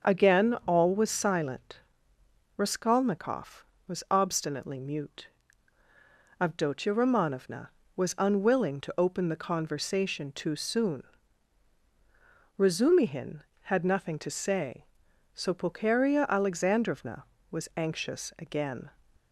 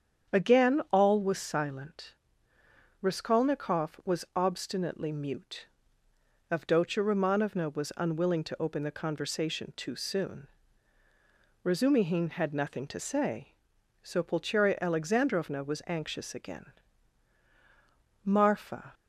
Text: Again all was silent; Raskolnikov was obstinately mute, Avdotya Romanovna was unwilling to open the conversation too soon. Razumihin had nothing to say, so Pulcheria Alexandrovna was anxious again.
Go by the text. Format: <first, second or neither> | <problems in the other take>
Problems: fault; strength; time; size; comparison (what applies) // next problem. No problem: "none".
first | starts louder than the rest; strong; until 1.4 s; 8 dB; also in the first // goes on to say "Marfa"; noticeable; from 18.2 s on; 0.68 s long